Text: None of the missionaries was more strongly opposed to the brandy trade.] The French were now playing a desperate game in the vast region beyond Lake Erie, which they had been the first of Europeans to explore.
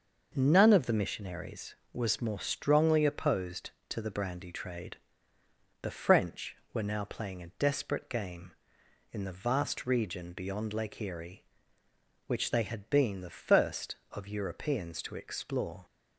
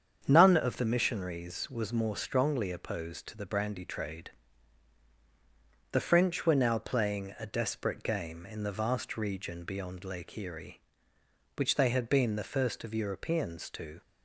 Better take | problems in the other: first | starts louder than the rest; strong; until 1.2 s; 7.5 dB // stops before "explore"; at 14.0 s

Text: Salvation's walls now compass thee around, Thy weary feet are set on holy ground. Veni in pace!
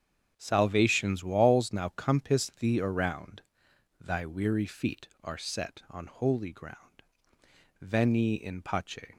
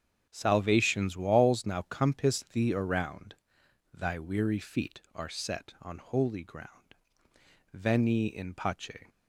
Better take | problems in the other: neither | starts louder than the rest; strong; the same in both

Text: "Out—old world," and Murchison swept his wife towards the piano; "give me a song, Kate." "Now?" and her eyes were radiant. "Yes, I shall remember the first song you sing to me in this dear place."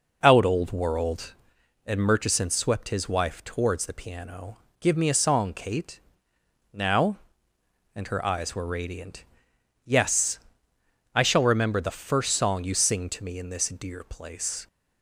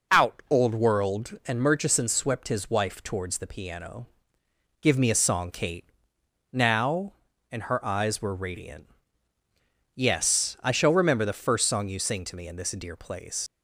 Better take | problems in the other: first | leaves "place" unfinished; at 13.4 s; 75 ms

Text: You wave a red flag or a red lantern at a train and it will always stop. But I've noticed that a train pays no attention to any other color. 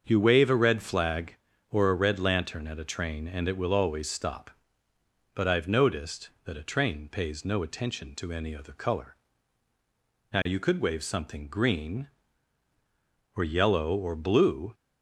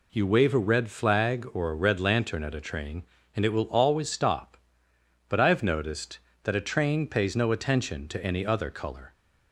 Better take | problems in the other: second | starts louder than the rest; until 1.0 s; 7 dB // goes on to say "Now you could wave something green or yellow or blue"; strong; from 10.3 s on; 4.4 s long

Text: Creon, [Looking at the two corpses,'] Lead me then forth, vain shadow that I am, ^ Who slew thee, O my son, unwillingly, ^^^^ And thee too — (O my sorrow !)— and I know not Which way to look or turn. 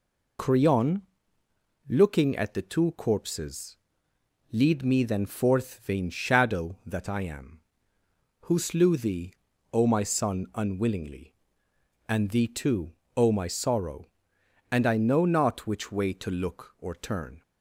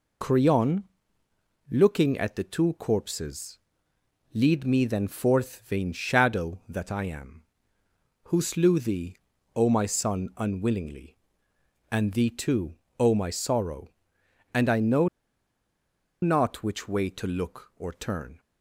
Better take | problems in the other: first | pauses between "know" and "not"; at 15.0 s; 1.1 s long

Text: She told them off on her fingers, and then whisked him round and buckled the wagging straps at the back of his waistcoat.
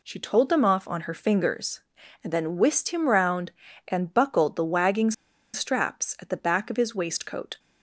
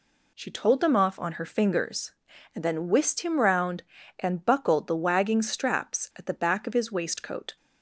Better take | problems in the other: second | pauses between "wagging" and "straps"; at 5.1 s; 0.41 s long

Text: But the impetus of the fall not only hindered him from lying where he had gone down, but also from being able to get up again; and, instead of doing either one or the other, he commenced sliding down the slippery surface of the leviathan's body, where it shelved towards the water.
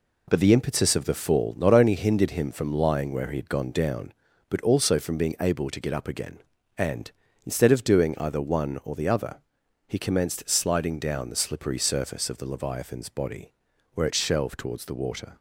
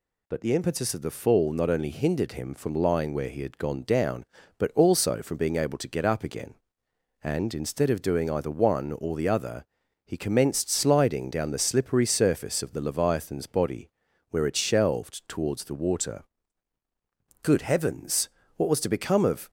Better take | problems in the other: first | goes on to say "Good heavens what was to become of"; strong; from 17.4 s on; 2.0 s long

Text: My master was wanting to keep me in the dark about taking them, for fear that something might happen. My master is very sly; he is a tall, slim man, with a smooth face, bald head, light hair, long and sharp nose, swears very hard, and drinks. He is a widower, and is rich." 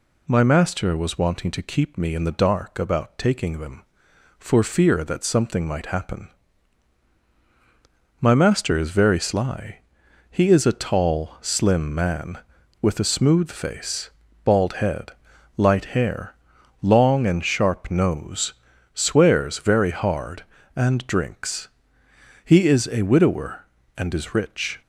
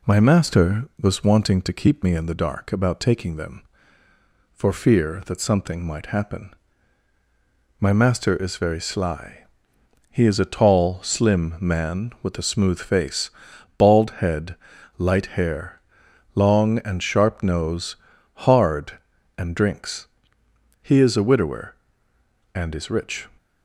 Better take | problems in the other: first | skips "swears very"; at 18.1 s

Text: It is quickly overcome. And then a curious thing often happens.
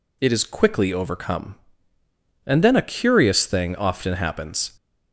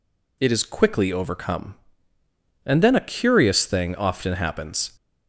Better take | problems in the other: neither | none

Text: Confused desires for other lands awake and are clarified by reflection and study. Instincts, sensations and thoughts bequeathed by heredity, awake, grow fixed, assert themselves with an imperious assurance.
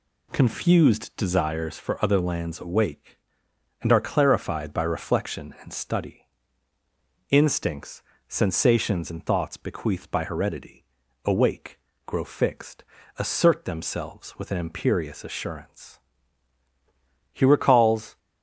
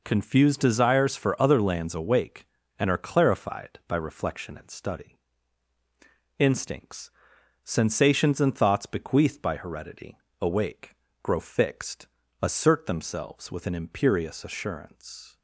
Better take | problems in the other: second | goes on to say "He recalls"; noticeable; from 17.3 s on; 0.86 s long

